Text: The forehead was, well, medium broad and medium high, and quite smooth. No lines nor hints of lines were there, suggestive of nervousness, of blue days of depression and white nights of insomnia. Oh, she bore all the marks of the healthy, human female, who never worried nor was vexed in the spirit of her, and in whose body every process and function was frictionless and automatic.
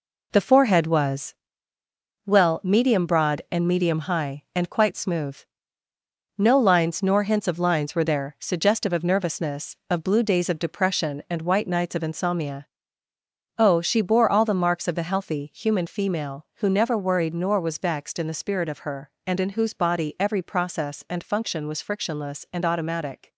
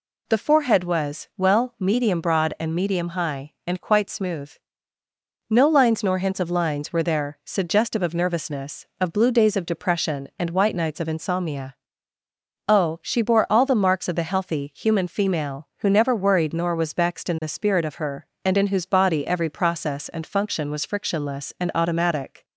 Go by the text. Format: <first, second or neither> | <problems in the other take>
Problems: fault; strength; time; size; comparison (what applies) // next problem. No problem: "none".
second | gets quieter; throughout; 6.5 dB